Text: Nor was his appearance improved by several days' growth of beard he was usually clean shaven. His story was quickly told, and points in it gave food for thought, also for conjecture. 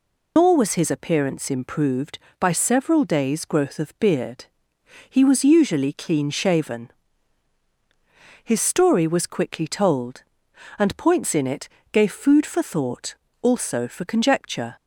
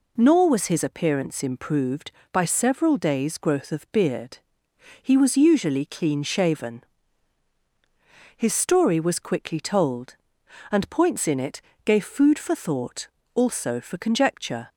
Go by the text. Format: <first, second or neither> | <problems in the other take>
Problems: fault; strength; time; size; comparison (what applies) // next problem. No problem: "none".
second | loses the start of "Nor"; at 0.3 s; 120 ms // pauses between "beard" and "he"; noticeable; at 4.4 s; 0.64 s long; noticeable in the second // pauses between "it" and "gave"; slight; at 11.6 s; 0.24 s long; slight in the second